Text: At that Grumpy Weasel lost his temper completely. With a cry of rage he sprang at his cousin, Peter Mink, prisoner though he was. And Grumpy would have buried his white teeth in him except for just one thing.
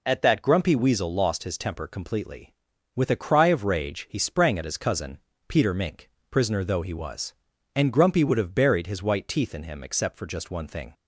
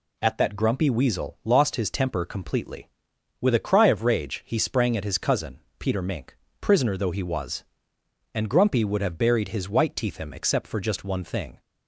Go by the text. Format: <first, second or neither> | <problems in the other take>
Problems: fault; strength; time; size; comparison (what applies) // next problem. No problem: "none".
first | skips "in"; at 10.1 s